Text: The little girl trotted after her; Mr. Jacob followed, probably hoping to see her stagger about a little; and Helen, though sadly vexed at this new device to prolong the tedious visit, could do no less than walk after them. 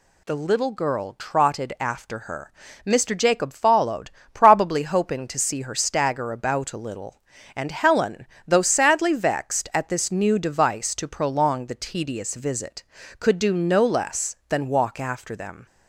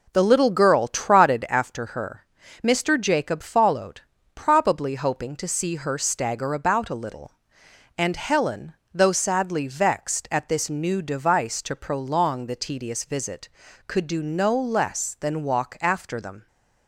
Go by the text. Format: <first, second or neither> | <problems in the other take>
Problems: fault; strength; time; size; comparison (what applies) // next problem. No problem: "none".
first | starts louder than the rest; noticeable; until 1.8 s; 4 dB